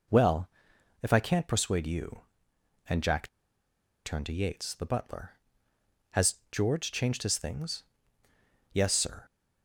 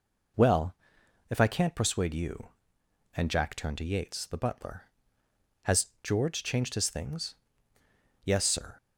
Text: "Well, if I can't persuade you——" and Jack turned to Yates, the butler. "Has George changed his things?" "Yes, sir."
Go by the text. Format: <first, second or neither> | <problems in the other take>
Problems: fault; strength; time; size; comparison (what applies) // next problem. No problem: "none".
second | pauses between "Jack" and "turned"; noticeable; at 3.2 s; 0.77 s long // pauses between "Has" and "George"; slight; at 6.3 s; 0.16 s long; slight in the second